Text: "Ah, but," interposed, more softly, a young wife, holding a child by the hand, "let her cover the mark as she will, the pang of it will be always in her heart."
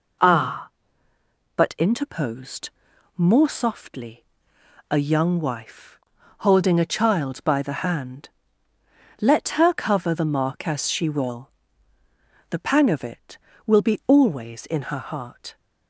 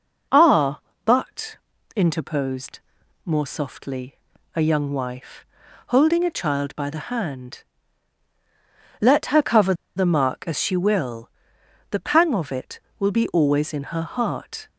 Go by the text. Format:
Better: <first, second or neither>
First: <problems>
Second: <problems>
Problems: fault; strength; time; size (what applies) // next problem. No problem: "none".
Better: first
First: none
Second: pauses between "cover" and "the"; slight; at 9.7 s; 0.23 s long